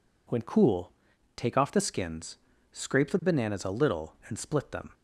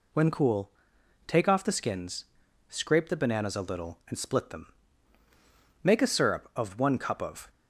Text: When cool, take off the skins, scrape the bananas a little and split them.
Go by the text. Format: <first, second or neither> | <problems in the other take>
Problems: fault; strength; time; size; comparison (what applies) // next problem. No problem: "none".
first | goes on to say "Make a syrup of one cup of"; from 5.8 s on; 1.6 s long